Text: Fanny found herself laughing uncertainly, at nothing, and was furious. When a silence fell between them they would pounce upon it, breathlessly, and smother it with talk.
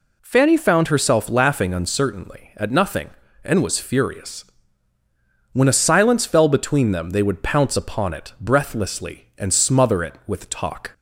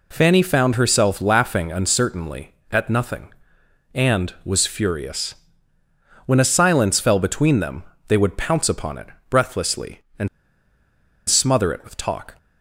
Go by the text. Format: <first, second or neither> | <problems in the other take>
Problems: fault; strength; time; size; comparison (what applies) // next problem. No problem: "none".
first | pauses between "them" and "they"; slight; at 7.8 s; 0.24 s long // pauses between "and" and "smother"; at 10.2 s; 0.99 s long